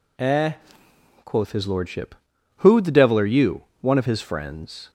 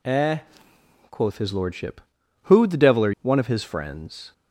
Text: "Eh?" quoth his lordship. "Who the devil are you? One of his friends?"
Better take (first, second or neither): first